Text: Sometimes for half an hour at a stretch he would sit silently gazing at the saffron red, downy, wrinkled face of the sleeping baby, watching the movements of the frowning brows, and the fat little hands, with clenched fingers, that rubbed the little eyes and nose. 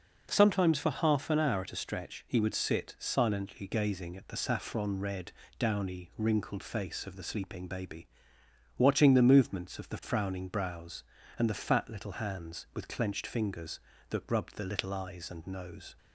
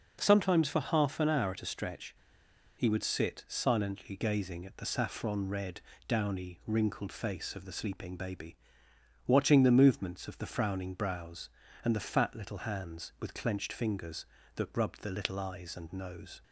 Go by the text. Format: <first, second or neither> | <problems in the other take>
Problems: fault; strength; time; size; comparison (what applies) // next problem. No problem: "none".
first | pauses between "stretch" and "he"; noticeable; at 2.1 s; 0.63 s long